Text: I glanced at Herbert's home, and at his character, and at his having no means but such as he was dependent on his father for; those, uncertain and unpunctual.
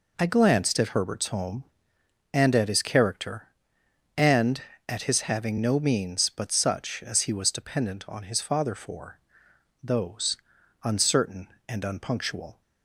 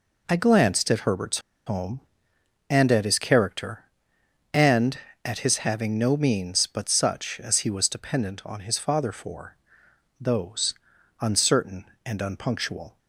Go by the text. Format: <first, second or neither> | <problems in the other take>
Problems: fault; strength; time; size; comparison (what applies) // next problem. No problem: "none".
first | pauses between "Herbert's" and "home"; slight; at 1.3 s; 0.27 s long